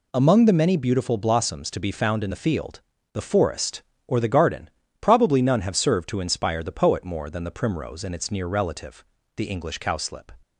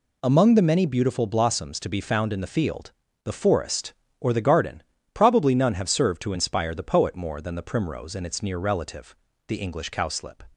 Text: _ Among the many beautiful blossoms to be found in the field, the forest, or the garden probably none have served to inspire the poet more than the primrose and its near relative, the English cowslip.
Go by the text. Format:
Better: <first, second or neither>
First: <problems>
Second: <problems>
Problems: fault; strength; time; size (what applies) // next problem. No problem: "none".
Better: neither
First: pauses between "garden" and "probably"; slight; at 4.6 s; 0.32 s long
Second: pauses between "garden" and "probably"; slight; at 4.8 s; 0.32 s long